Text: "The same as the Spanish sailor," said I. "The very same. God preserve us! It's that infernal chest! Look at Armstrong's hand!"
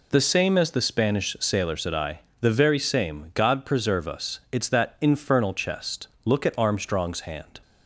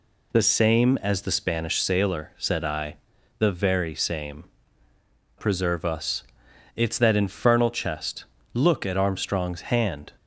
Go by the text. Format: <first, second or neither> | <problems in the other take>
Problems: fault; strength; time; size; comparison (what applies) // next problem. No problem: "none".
first | skips "God"; at 4.9 s